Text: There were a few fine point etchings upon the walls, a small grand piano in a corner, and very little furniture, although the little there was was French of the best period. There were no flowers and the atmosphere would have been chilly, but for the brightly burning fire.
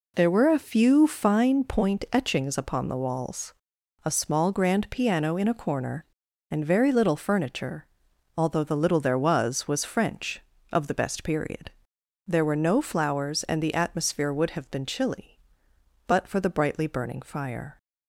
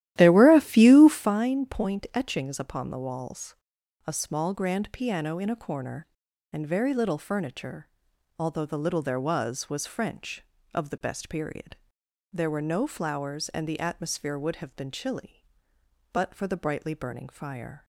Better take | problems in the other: first | starts louder than the rest; strong; until 1.3 s; 13.5 dB

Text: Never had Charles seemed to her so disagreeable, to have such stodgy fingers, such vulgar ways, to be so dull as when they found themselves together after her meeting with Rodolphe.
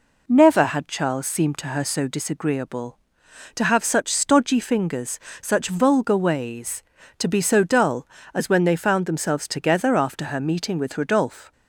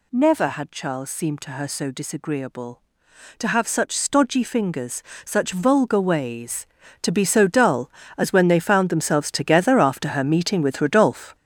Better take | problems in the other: first | gets louder; throughout; 7 dB

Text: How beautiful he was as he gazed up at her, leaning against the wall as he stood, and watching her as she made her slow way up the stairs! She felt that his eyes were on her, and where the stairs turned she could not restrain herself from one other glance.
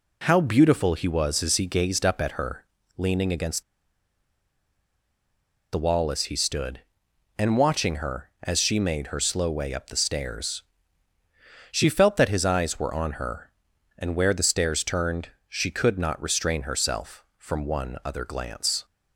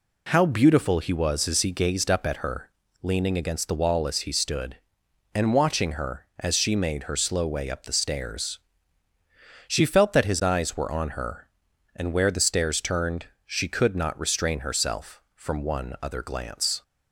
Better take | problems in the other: second | pauses between "against" and "the"; strong; at 3.6 s; 2.0 s long // pauses between "turned" and "she"; slight; at 15.3 s; 0.18 s long; slight in the second

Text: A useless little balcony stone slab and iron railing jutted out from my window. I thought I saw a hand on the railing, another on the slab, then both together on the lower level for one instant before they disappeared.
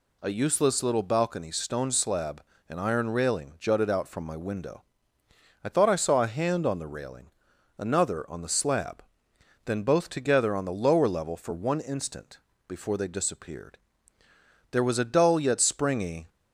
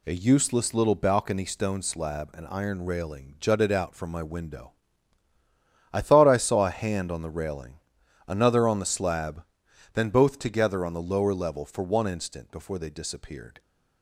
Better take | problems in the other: second | pauses between "instant" and "before"; slight; at 12.3 s; 0.28 s long // goes on to say "There was a dull yet springy"; from 14.7 s on; 1.5 s long

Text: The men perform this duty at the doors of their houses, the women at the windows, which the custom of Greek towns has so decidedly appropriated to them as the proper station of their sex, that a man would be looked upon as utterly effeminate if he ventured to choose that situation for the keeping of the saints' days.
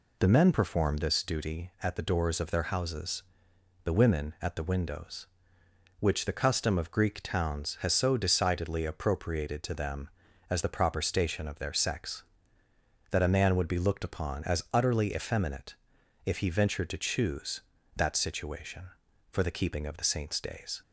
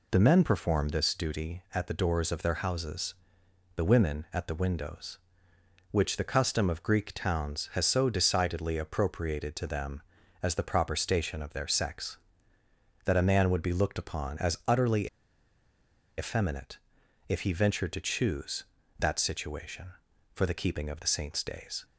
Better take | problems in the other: first | pauses between "utterly" and "effeminate"; at 15.0 s; 1.0 s long // pauses between "effeminate" and "if"; noticeable; at 16.7 s; 0.50 s long; noticeable in the first

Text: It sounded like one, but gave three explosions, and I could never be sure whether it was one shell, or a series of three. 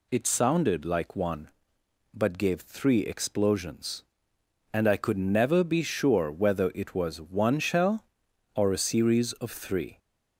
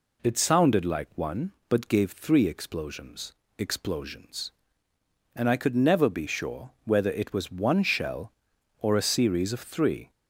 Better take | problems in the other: first | says "explosions" twice; at 3.5 s // pauses between "sure" and "whether"; slight; at 6.6 s; 0.16 s long

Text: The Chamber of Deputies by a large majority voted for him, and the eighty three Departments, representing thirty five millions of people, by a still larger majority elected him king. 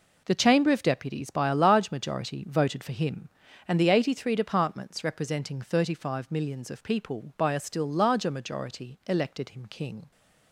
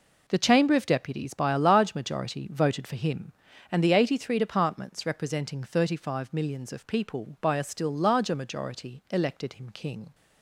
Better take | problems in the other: neither | none

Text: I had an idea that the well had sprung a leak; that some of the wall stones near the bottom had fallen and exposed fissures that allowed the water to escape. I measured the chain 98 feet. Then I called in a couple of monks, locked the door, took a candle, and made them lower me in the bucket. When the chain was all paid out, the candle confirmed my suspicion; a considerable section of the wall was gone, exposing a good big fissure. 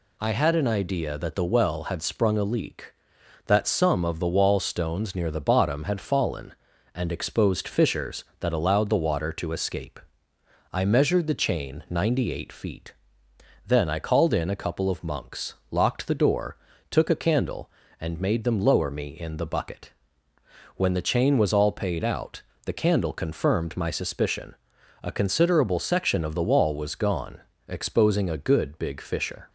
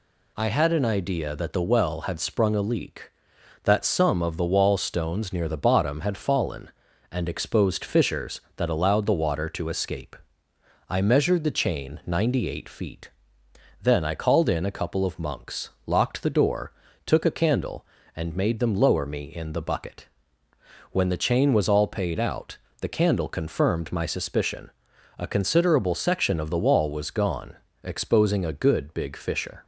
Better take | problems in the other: neither | none

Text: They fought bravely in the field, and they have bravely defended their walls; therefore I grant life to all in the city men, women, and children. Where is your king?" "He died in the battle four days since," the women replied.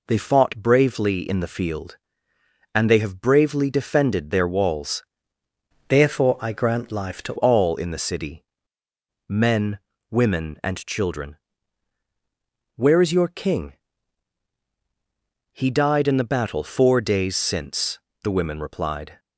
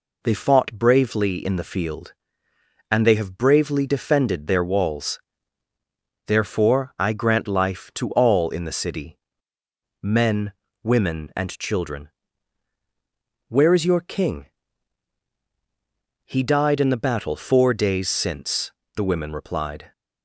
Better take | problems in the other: second | changes voice from "therefore" to "to"; from 5.8 to 7.3 s; 1.5 s long // pauses between "city" and "men"; noticeable; at 8.4 s; 0.86 s long; noticeable in the second

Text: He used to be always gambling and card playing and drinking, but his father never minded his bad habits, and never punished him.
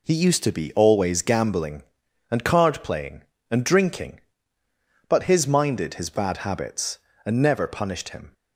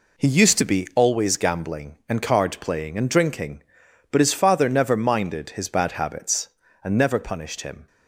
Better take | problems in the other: second | skips "father never"; at 5.4 s

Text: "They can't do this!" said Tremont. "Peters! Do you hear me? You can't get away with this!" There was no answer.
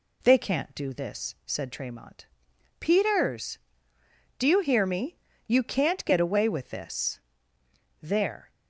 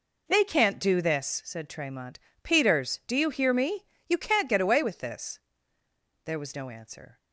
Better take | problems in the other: second | stops before "was no answer"; at 8.5 s

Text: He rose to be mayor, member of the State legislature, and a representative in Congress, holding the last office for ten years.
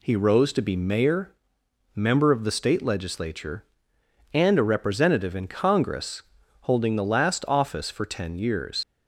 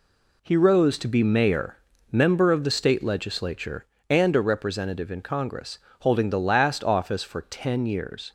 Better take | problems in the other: second | leaves "years" unfinished; at 8.8 s; 70 ms

